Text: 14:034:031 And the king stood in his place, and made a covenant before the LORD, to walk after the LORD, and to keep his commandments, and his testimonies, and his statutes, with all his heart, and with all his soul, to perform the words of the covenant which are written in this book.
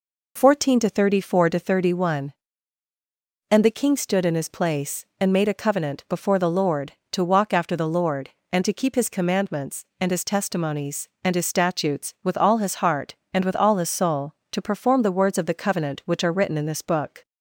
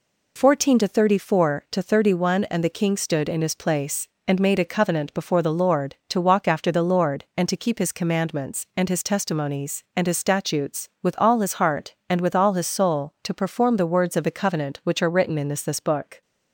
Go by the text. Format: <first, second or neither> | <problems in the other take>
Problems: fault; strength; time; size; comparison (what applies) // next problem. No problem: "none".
first | says "this" twice; at 15.6 s